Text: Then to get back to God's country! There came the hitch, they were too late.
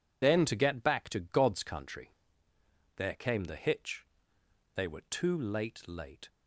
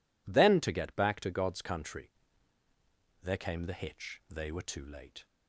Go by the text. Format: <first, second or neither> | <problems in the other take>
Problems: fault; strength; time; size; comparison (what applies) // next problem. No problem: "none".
second | says "late" twice; at 5.8 s